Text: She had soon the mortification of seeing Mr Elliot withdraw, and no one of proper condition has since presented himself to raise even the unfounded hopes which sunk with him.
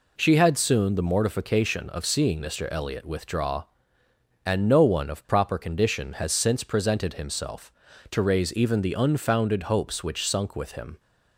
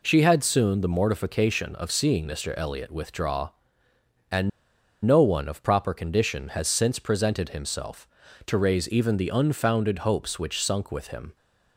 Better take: first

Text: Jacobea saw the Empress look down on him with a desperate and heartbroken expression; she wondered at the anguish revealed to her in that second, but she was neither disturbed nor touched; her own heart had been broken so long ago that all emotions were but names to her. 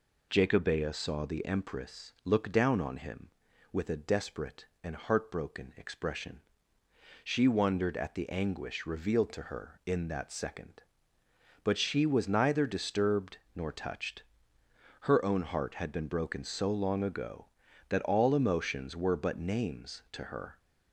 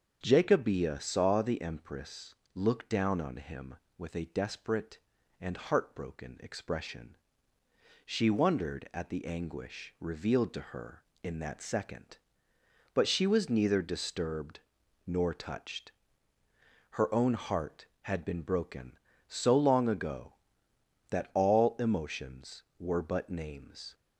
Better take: first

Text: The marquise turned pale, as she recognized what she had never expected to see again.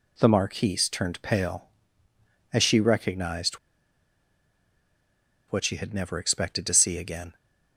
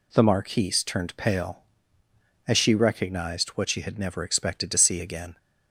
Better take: second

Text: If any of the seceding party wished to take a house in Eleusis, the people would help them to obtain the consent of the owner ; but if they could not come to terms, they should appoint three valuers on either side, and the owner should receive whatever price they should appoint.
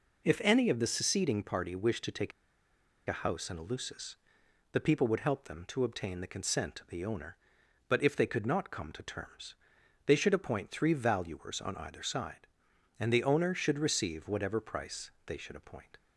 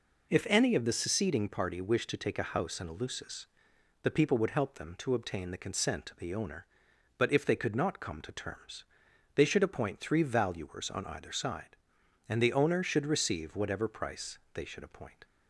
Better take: second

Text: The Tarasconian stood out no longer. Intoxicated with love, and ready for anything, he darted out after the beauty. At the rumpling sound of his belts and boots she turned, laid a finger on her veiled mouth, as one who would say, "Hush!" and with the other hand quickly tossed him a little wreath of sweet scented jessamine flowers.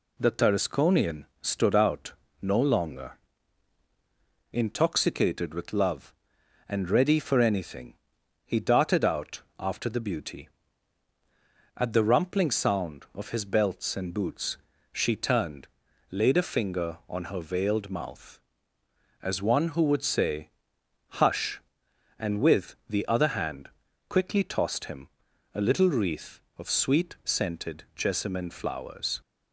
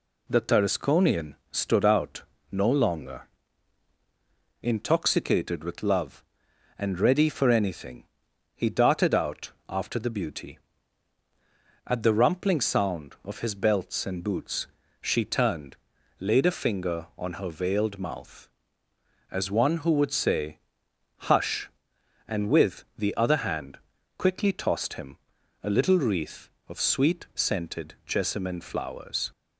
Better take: neither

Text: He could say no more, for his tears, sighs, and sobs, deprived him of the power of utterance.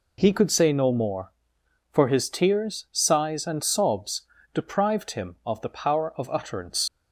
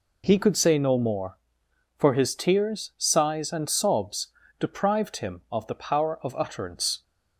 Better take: second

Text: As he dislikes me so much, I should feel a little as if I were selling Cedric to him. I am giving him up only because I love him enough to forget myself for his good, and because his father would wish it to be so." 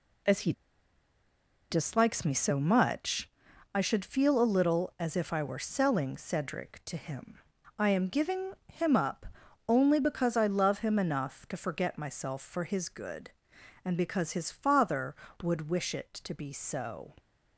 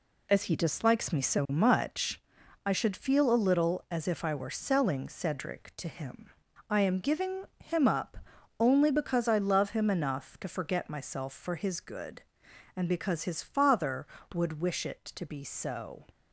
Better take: second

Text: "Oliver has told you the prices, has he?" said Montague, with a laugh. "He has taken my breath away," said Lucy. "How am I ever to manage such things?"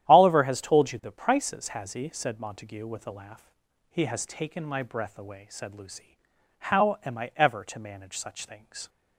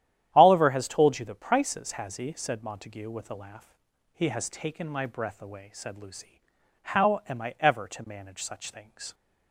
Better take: neither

